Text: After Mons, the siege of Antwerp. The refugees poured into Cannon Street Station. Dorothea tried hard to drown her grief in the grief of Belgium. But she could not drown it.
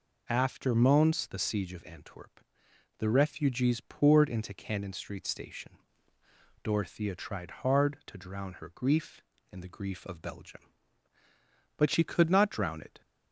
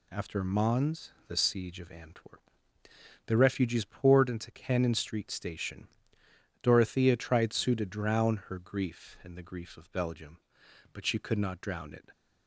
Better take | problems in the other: first | says "sue" for "hard"; at 7.5 s

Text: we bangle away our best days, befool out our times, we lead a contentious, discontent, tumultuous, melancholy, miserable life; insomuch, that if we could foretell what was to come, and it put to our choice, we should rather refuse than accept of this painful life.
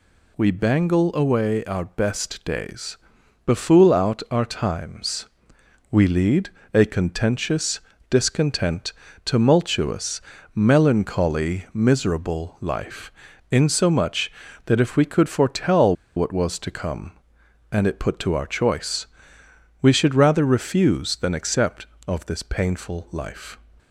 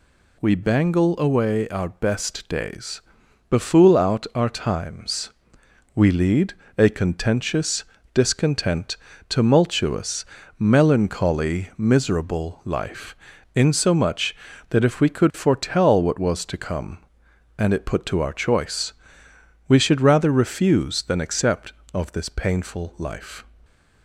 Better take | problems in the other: second | pauses between "lead" and "a"; slight; at 6.4 s; 0.24 s long; slight in the second // pauses between "foretell" and "what"; slight; at 15.9 s; 0.22 s long

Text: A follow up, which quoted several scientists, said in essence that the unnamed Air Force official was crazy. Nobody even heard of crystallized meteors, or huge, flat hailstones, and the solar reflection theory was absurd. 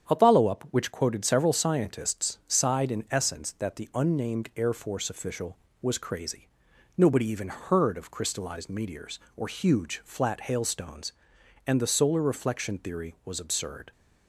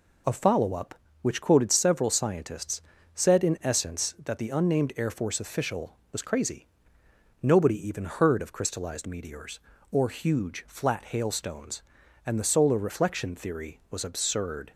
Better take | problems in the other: second | starts louder than the rest; strong; until 1.1 s; 8.5 dB // says "sighed" for "said"; at 2.4 s

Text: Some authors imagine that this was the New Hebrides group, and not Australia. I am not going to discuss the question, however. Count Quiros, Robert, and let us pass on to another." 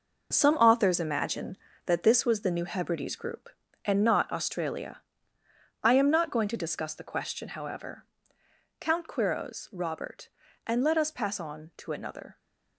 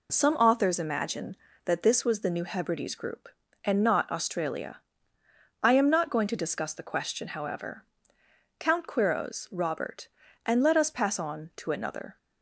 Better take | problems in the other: second | gets quieter; strong; throughout; 8.5 dB

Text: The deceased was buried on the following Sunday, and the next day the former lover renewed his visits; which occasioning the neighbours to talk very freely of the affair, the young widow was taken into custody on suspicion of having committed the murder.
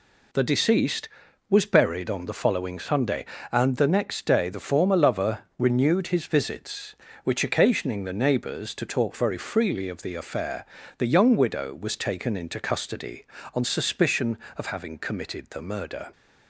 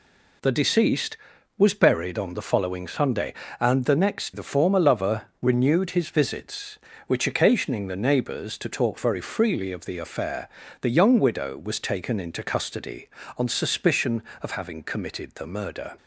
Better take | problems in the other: first | skips "day"; at 4.3 s // pauses between "lover" and "renewed"; slight; at 5.2 s; 0.20 s long; slight in the first

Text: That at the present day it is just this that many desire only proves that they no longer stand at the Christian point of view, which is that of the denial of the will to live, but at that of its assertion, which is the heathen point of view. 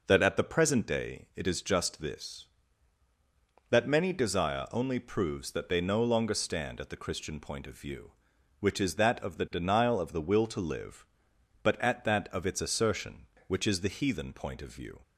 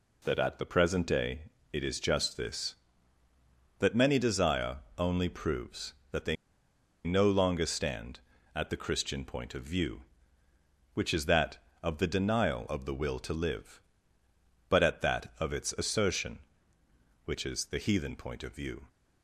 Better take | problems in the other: first | pauses between "day" and "it"; slight; at 1.4 s; 0.32 s long // pauses between "desire" and "only"; slight; at 4.7 s; 0.20 s long // pauses between "they" and "no"; noticeable; at 6.3 s; 0.70 s long

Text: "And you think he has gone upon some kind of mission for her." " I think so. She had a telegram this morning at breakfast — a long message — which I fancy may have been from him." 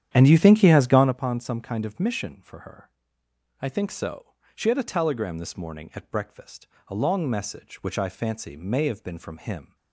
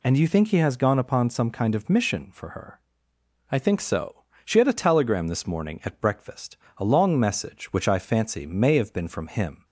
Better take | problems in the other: second | starts louder than the rest; strong; until 1.2 s; 10 dB

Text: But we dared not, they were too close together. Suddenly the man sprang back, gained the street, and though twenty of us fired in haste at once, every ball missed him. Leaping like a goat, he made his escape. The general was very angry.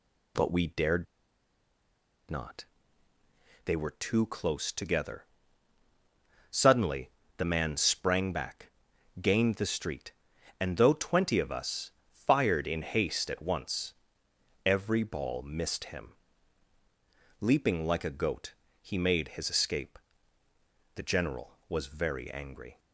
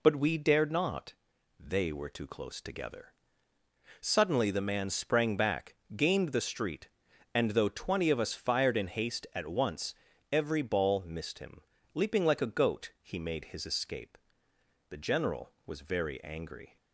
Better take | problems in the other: second | pauses between "dared" and "not"; strong; at 1.0 s; 1.2 s long // pauses between "Suddenly" and "the"; slight; at 7.0 s; 0.26 s long // pauses between "us" and "fired"; slight; at 11.9 s; 0.18 s long

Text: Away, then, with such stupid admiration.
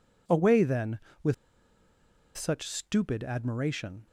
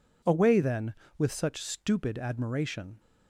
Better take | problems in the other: second | pauses between "with" and "such"; at 1.3 s; 1.0 s long

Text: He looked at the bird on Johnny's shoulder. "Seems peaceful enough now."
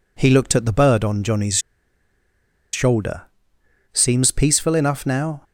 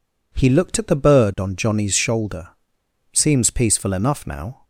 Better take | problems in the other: second | pauses between "Johnny's" and "shoulder"; at 1.5 s; 1.1 s long

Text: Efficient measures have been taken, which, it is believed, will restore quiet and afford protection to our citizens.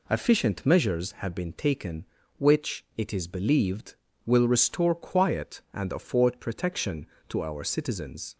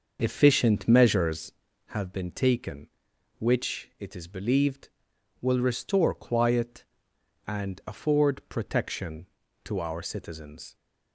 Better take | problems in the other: first | starts louder than the rest; until 1.7 s; 6.5 dB

